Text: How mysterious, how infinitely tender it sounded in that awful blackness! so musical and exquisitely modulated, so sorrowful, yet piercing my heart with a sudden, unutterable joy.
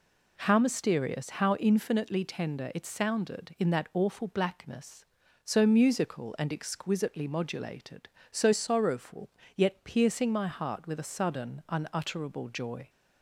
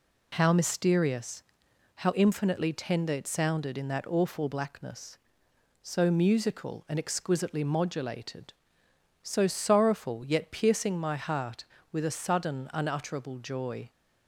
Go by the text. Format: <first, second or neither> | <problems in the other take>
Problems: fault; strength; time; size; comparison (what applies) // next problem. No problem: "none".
neither | none